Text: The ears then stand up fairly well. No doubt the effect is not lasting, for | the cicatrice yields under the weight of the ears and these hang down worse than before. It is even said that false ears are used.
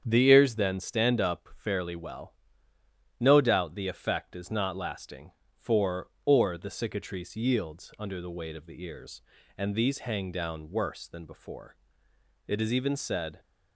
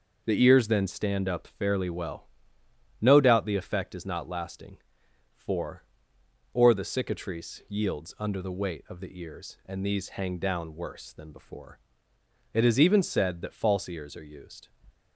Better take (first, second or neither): second